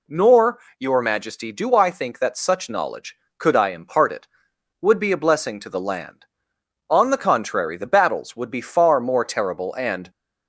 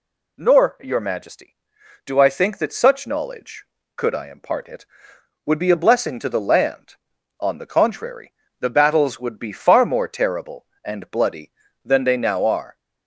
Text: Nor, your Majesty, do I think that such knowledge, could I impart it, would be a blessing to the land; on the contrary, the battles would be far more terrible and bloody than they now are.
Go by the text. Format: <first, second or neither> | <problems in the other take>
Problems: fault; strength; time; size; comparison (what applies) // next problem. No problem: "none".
second | stops before "bloody than they now are"; at 10.0 s